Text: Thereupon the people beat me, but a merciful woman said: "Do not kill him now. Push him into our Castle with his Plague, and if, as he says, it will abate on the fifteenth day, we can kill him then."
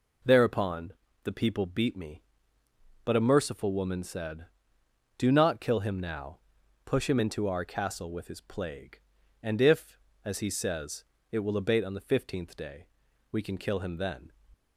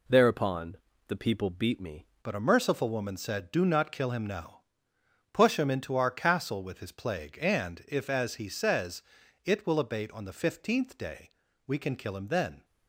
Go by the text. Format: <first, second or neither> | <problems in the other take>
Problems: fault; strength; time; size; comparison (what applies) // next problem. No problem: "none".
first | pauses between "Thereupon" and "the"; slight; at 0.7 s; 0.32 s long; slight in the first // changes voice at "but"; from 2.2 s on; 10.4 s long